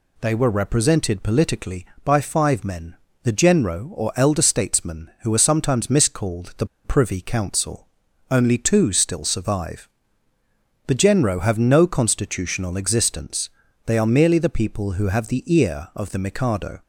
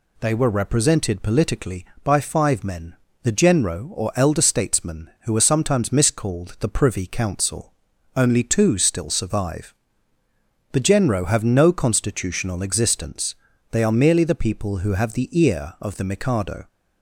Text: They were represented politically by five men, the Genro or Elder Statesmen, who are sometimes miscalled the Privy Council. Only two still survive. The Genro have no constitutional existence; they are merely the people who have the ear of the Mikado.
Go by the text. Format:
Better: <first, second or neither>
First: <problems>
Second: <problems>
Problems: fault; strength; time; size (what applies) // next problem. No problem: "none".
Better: second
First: pauses between "the" and "Privy"; slight; at 6.6 s; 0.19 s long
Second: none